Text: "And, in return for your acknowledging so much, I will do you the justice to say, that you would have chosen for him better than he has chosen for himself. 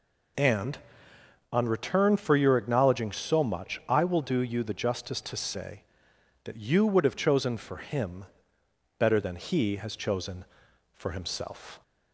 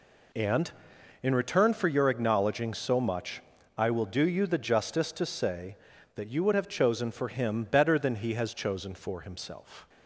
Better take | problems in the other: second | says "on" for "in"; at 1.5 s // pauses between "him" and "better"; noticeable; at 8.2 s; 0.72 s long

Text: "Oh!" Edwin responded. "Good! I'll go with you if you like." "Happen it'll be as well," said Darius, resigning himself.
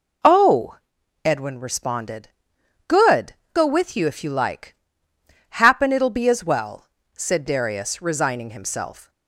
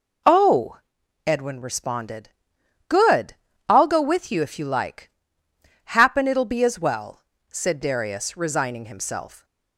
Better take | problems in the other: second | skips "I'll"; at 3.4 s

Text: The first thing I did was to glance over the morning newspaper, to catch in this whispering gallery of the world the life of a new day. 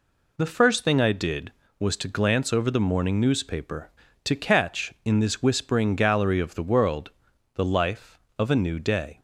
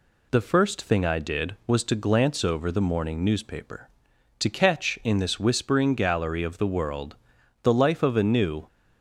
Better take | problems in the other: first | pauses between "world" and "the"; noticeable; at 7.1 s; 0.48 s long; also in the first // stops before "day"; at 8.6 s

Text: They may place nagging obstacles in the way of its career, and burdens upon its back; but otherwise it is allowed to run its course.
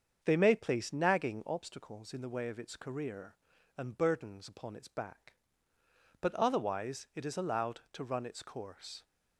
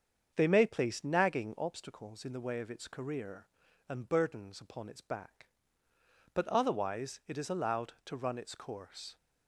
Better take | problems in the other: neither | starts louder than the rest; strong; the same in both

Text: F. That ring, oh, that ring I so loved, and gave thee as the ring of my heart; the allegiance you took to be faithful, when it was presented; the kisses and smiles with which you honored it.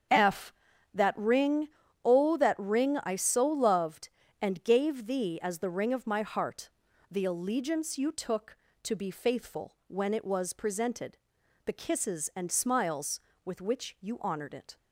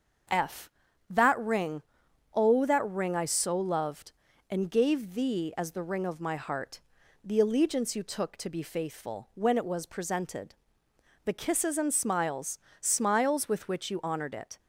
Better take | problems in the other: first | starts louder than the rest; until 1.7 s; 7 dB; strong in the first // says "smiles" twice; at 12.7 s

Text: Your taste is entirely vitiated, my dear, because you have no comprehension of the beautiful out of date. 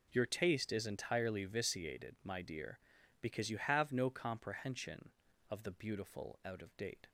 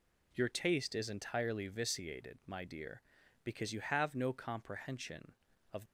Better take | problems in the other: first | stops before "the beautiful out of date"; at 5.8 s

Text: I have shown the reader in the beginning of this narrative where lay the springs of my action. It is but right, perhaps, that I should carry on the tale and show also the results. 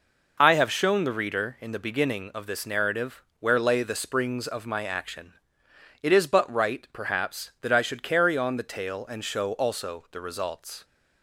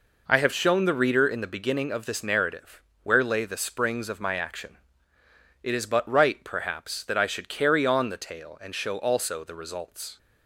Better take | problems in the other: neither | pauses between "narrative" and "where"; slight; the same in both

